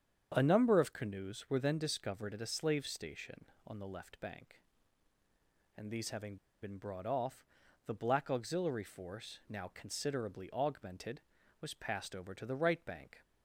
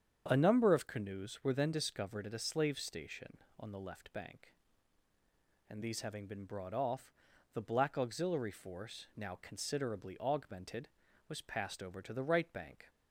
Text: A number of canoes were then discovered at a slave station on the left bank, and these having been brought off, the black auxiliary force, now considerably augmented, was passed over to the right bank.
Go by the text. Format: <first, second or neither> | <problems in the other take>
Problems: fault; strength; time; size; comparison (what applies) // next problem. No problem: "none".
second | starts louder than the rest; strong; until 1.3 s; 7.5 dB; strong in the second // pauses between "having" and "been"; slight; at 6.3 s; 0.25 s long